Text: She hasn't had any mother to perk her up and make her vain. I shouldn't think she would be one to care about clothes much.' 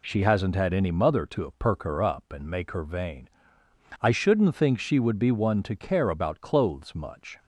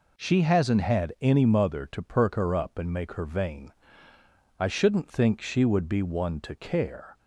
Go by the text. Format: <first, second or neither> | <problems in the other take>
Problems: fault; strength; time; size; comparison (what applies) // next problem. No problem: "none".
first | stops before "about clothes much"; at 7.1 s